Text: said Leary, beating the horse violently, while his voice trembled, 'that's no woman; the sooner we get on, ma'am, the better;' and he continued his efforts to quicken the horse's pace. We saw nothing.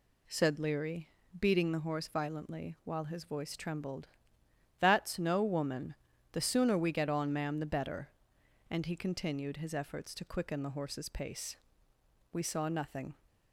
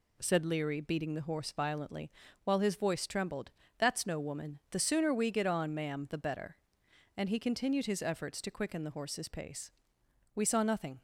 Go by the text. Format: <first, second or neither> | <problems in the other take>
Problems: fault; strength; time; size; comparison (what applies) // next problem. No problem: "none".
neither | none